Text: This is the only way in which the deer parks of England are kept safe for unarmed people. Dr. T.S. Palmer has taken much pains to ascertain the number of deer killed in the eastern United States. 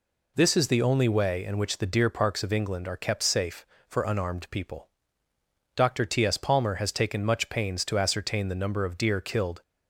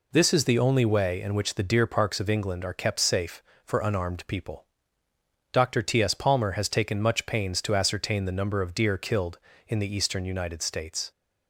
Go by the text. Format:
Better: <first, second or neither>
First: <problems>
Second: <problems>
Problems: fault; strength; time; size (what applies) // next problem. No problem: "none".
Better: second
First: stops before "in the eastern United States"; at 9.6 s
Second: none